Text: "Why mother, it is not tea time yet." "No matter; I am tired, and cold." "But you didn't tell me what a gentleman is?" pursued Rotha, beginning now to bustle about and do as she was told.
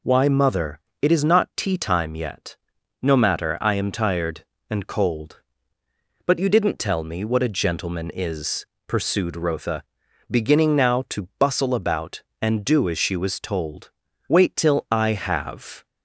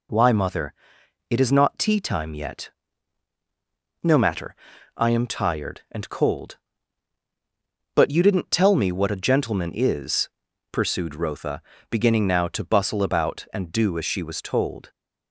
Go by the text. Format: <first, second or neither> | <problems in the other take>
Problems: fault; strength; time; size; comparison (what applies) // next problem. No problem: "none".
second | goes on to say "Wait till I have"; from 14.2 s on; 1.5 s long